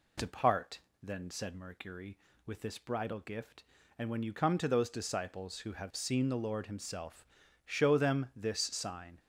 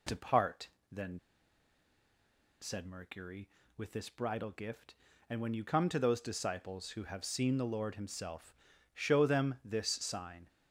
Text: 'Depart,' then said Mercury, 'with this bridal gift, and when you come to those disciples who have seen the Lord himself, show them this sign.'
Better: first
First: none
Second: pauses between "then" and "said"; strong; at 1.1 s; 1.4 s long

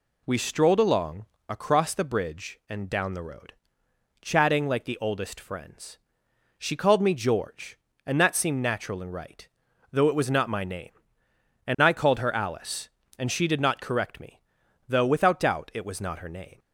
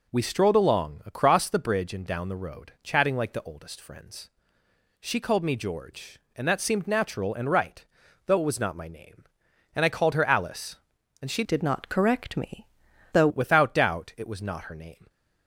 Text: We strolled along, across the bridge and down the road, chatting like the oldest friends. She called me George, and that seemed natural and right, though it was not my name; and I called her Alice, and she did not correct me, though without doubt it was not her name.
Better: first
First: none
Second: changes voice from "did" to "though"; from 11.4 to 13.2 s; 1.8 s long

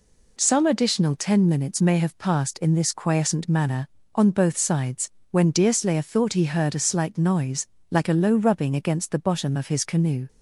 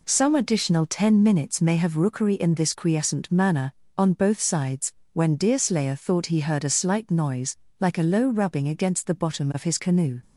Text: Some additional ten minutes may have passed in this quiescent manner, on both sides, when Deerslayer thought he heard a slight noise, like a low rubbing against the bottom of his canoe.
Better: first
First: none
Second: says "rookery" for "passed"; at 1.9 s

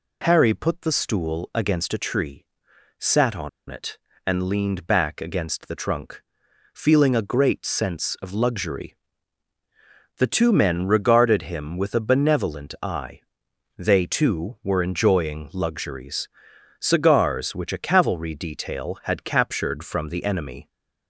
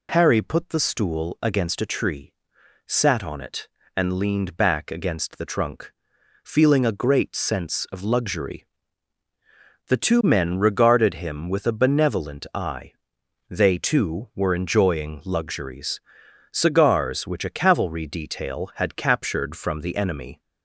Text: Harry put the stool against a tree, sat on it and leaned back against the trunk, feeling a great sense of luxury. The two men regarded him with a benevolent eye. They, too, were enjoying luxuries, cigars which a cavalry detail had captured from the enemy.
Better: second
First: pauses between "on" and "it"; slight; at 3.4 s; 0.20 s long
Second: none

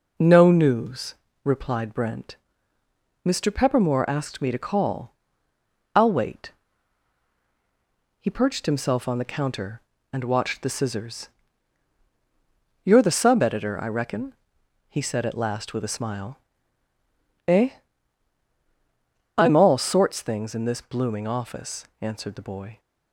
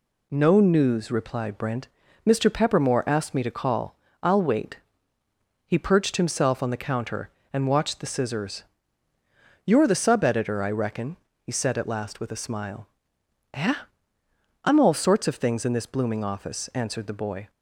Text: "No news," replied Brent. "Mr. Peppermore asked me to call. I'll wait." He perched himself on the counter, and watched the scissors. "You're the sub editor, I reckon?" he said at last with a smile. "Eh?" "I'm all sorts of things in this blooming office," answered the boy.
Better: second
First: skips "of"; at 20.2 s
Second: none

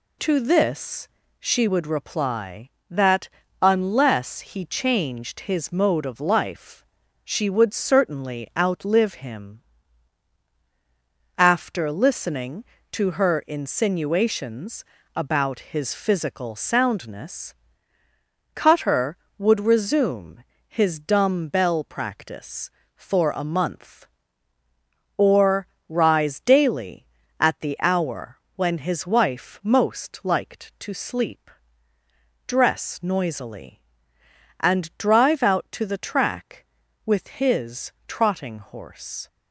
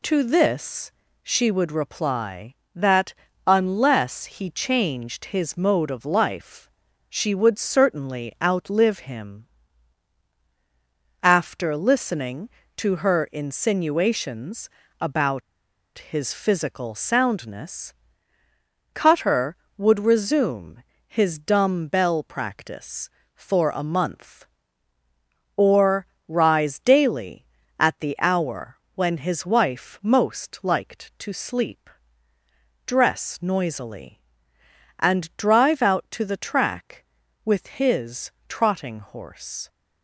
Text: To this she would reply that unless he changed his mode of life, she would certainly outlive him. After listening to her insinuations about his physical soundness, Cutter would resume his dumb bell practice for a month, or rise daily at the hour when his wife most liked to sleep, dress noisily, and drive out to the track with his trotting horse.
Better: first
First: pauses between "this" and "she"; slight; at 1.0 s; 0.30 s long // pauses between "that" and "unless"; slight; at 3.2 s; 0.32 s long // pauses between "insinuations" and "about"; slight; at 14.8 s; 0.32 s long // pauses between "resume" and "his"; slight; at 20.4 s; 0.24 s long // pauses between "or" and "rise"; slight; at 25.6 s; 0.22 s long // pauses between "hour" and "when"; slight; at 28.3 s; 0.18 s long // pauses between "his" and "trotting"; slight; at 37.9 s; 0.16 s long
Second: pauses between "this" and "she"; slight; at 0.9 s; 0.30 s long // pauses between "that" and "unless"; slight; at 3.1 s; 0.32 s long // pauses between "insinuations" and "about"; slight; at 14.6 s; 0.32 s long // pauses between "about" and "his"; noticeable; at 15.4 s; 0.57 s long // pauses between "resume" and "his"; slight; at 20.8 s; 0.24 s long // pauses between "or" and "rise"; slight; at 26.0 s; 0.22 s long // pauses between "hour" and "when"; slight; at 28.7 s; 0.18 s long // pauses between "his" and "trotting"; slight; at 38.3 s; 0.18 s long

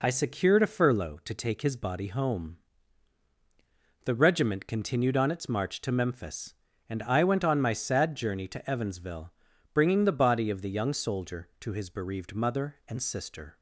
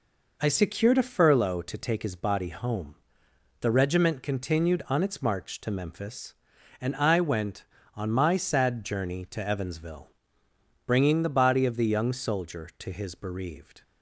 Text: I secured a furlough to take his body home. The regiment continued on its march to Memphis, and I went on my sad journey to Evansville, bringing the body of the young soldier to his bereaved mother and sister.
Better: first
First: none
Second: stops before "mother and sister"; at 13.8 s

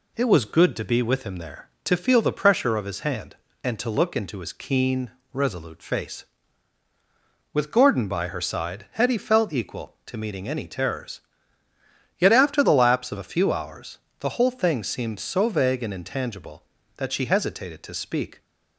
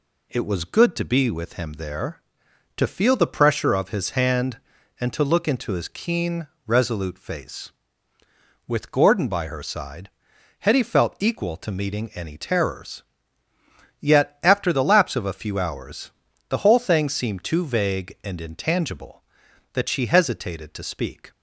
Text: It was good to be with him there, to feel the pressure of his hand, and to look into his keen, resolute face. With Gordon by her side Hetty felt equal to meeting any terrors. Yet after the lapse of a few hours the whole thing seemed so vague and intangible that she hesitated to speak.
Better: first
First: pauses between "hours" and "the"; slight; at 13.9 s; 0.22 s long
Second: pauses between "side" and "Hetty"; noticeable; at 10.1 s; 0.50 s long // pauses between "hours" and "the"; at 16.1 s; 0.38 s long // says "too" for "so"; at 17.4 s

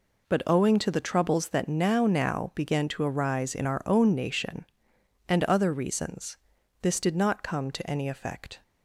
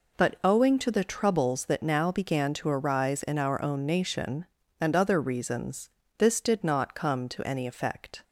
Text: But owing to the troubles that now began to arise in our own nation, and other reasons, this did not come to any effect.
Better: second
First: says "now" twice; at 2.0 s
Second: none

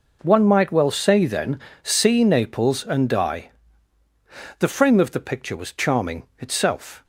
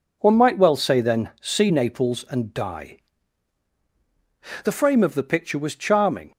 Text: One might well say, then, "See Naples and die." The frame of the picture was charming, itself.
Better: first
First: none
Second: stops before "itself"; at 6.3 s

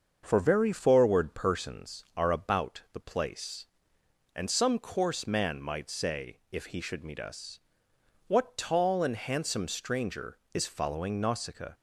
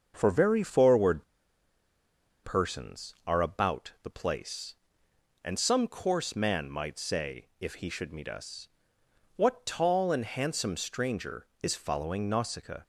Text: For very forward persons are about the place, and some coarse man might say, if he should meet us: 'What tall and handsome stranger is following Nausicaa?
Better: first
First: starts louder than the rest; until 1.2 s; 6.5 dB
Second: starts louder than the rest; until 1.1 s; 6.5 dB // pauses between "forward" and "persons"; at 1.2 s; 1.2 s long

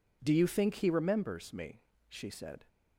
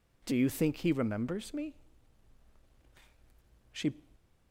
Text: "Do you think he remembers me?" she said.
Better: first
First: none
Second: stops before "said"; at 4.1 s

